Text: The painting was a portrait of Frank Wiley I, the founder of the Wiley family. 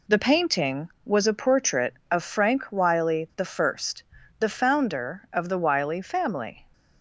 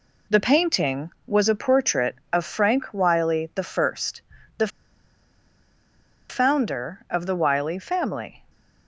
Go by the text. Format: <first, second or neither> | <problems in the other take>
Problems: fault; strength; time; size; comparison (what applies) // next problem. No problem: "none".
first | pauses between "the" and "founder"; strong; at 4.6 s; 1.6 s long